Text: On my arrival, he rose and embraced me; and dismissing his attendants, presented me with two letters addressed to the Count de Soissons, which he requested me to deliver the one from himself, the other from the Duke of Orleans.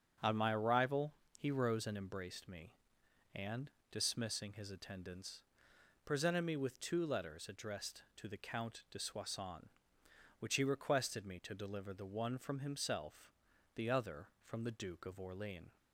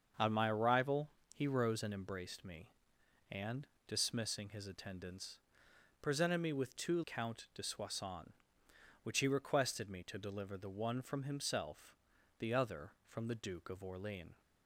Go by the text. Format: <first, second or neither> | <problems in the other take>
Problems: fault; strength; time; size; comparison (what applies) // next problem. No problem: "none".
first | starts louder than the rest; until 1.4 s; 6.5 dB; strong in the first // pauses between "and" and "dismissing"; slight; at 3.6 s; 0.18 s long; slight in the first // skips "letters addressed to the"; at 7.0 s